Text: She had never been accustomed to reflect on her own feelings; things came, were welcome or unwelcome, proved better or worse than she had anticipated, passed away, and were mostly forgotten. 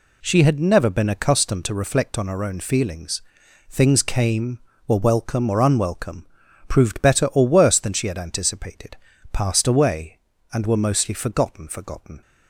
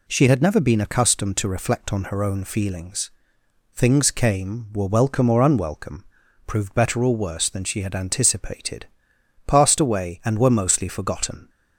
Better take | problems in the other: second | says "forgotten" twice; at 11.6 s

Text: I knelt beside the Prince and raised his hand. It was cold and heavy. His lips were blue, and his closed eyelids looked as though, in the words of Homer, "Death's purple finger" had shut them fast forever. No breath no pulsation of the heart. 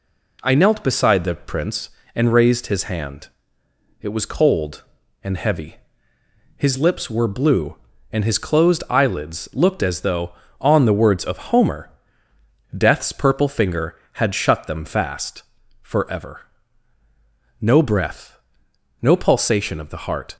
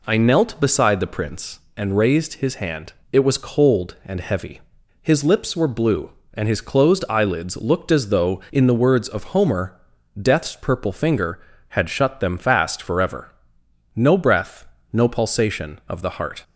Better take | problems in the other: second | says "on" for "in"; at 10.5 s // pauses between "fast" and "forever"; at 15.4 s; 0.40 s long // pauses between "breath" and "no"; noticeable; at 18.3 s; 0.66 s long; slight in the second

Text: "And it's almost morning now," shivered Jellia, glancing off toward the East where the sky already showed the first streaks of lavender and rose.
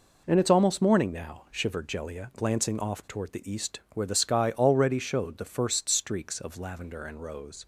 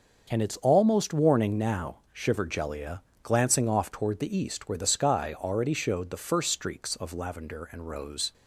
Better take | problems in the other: first | starts louder than the rest; until 1.3 s; 6 dB // says "warning" for "morning"; at 1.1 s

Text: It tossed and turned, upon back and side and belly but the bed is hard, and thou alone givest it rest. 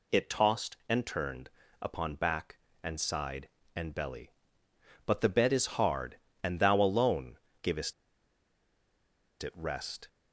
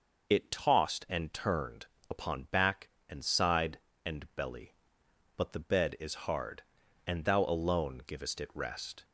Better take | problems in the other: second | pauses between "alone" and "givest"; slight; at 7.3 s; 0.26 s long // pauses between "givest" and "it"; strong; at 7.9 s; 1.4 s long

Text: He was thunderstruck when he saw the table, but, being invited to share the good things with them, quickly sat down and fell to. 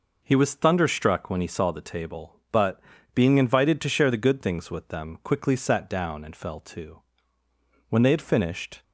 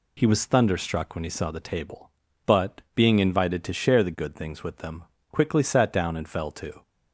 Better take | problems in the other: second | goes on to say "When they had finished"; noticeable; from 7.8 s on; 0.94 s long

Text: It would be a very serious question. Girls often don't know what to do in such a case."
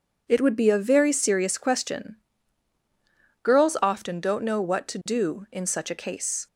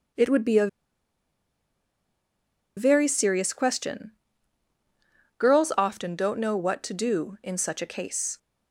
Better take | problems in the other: first | pauses between "a" and "very"; strong; at 0.6 s; 2.0 s long

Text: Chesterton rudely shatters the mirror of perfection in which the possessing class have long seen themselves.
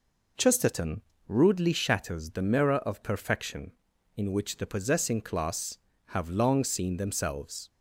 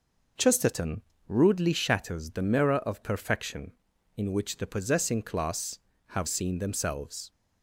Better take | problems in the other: first | pauses between "Chesterton" and "rudely"; slight; at 1.0 s; 0.28 s long; slight in the first // skips "long"; at 6.2 s

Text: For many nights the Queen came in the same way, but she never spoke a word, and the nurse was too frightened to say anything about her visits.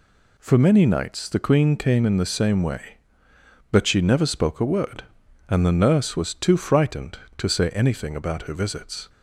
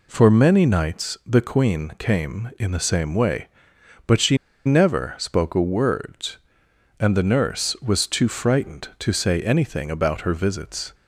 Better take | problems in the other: first | pauses between "she" and "never"; slight; at 4.3 s; 0.28 s long

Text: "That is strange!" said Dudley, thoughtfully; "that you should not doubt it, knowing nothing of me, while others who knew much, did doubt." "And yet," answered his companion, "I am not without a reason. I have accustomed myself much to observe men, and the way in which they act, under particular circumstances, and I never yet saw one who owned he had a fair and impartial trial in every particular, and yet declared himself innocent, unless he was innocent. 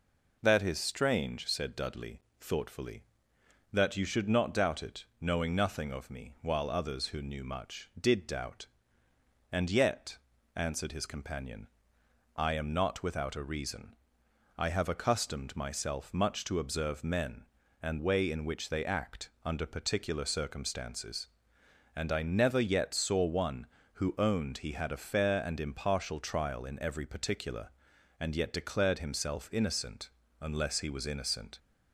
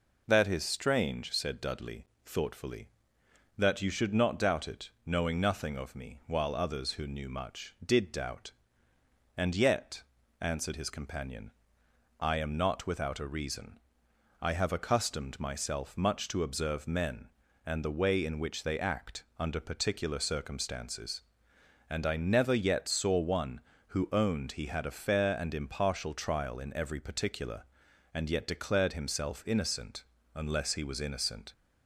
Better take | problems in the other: second | skips "the"; at 17.9 s

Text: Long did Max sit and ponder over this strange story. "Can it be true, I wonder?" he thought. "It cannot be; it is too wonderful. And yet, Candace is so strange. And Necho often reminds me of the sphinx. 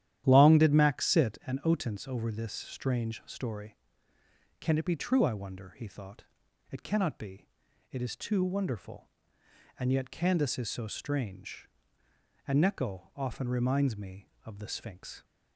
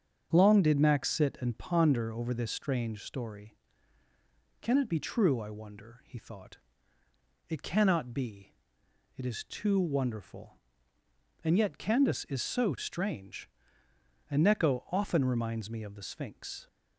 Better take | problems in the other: second | starts louder than the rest; strong; until 1.2 s; 11.5 dB; strong in the second // says "otence" for "ponder"; at 1.6 s

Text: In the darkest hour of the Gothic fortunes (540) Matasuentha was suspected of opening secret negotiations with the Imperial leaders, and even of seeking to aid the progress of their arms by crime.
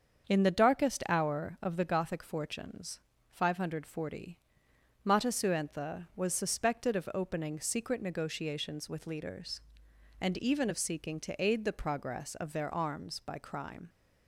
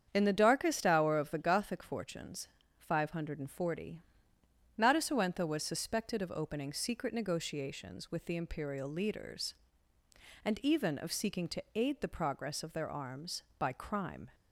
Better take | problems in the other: second | starts louder than the rest; until 1.3 s; 7 dB; strong in the second // skips "the Imperial"; at 9.0 s

